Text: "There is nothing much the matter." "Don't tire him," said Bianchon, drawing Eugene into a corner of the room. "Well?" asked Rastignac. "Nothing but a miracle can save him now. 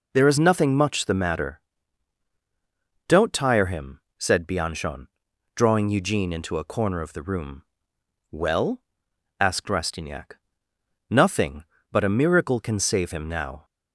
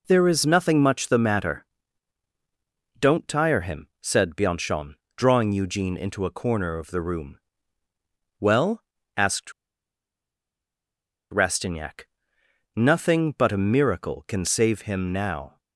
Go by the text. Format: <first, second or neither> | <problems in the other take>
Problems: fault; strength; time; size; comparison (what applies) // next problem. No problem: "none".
first | pauses between "asked" and "Rastignac"; strong; at 9.5 s; 1.7 s long